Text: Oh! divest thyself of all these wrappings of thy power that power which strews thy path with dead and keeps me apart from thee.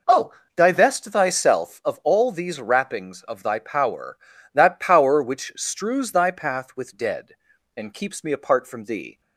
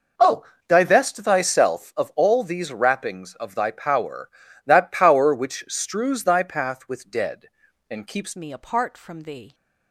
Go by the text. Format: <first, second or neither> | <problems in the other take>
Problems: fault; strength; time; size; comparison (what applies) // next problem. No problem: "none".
first | changes voice at "me"; from 8.3 s on; 1.2 s long